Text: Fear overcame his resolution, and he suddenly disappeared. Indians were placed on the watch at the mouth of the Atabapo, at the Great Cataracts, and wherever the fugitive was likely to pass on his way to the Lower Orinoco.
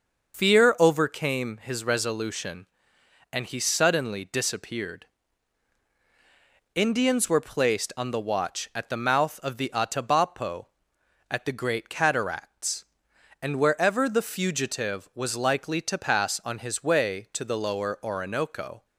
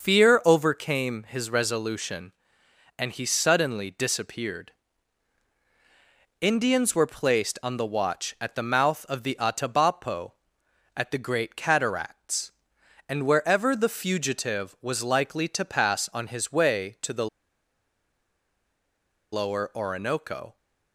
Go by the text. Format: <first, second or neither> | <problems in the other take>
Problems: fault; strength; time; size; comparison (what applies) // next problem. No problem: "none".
first | pauses between "the" and "Lower"; strong; at 17.2 s; 2.0 s long